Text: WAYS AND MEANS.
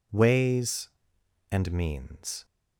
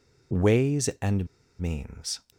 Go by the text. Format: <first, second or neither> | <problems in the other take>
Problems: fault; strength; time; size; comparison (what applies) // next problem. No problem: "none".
first | pauses between "AND" and "MEANS"; slight; at 1.2 s; 0.32 s long